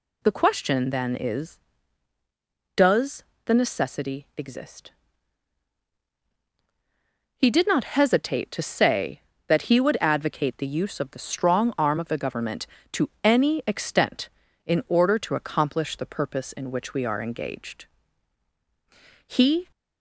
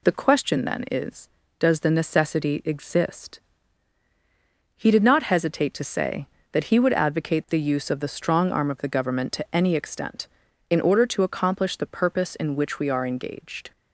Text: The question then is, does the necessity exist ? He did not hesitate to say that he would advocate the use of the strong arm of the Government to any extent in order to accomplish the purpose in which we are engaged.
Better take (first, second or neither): second